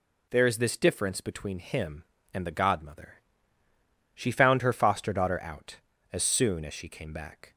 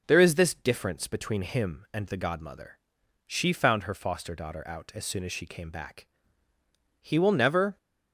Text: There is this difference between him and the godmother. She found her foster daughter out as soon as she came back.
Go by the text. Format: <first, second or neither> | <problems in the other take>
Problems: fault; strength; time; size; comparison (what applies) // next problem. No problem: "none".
first | goes on to say "He will never"; noticeable; from 7.0 s on; 0.76 s long